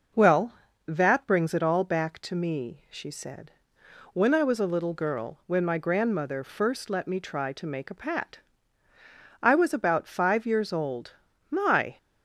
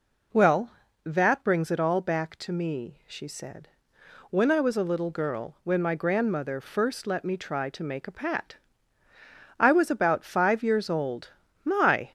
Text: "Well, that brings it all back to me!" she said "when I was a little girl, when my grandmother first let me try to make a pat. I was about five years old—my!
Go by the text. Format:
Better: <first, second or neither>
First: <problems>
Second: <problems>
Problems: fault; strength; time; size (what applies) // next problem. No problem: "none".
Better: first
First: pauses between "said" and "when"; noticeable; at 3.5 s; 0.62 s long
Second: gets louder; slight; throughout; 3 dB // pauses between "said" and "when"; noticeable; at 3.6 s; 0.62 s long